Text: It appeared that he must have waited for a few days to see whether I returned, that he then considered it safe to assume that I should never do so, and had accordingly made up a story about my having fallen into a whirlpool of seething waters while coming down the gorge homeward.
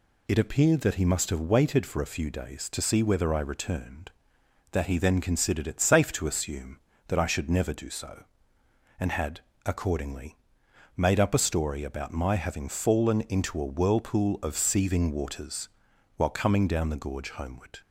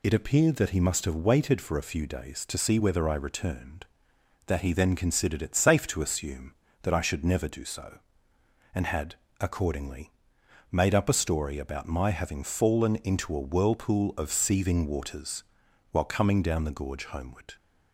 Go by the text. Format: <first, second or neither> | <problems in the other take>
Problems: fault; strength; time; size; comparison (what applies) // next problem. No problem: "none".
neither | pauses between "had" and "accordingly"; slight; the same in both // pauses between "accordingly" and "made"; noticeable; the same in both // pauses between "waters" and "while"; noticeable; the same in both